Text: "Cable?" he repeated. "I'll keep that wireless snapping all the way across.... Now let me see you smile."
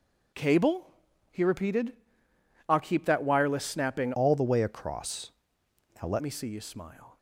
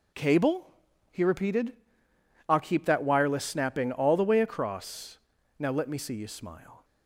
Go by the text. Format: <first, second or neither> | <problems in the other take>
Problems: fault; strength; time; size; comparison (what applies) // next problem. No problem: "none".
second | changes voice from "all" to "let"; from 4.1 to 6.2 s; 2.1 s long